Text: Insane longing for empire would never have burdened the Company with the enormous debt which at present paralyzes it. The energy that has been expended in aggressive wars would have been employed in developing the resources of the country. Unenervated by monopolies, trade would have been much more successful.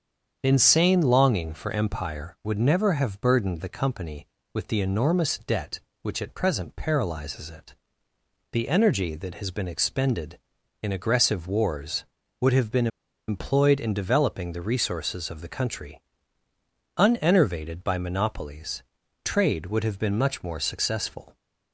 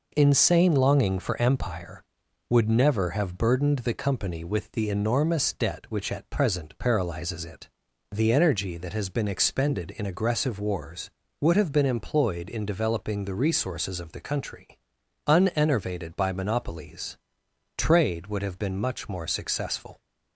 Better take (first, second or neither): second